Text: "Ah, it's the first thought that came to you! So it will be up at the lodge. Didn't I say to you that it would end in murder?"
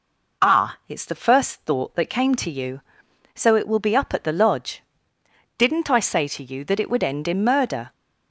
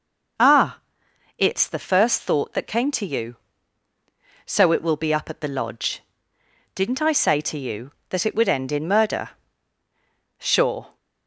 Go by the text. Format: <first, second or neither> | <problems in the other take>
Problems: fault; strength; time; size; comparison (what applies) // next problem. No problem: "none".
first | goes on to say "Sure"; from 10.3 s on; 0.58 s long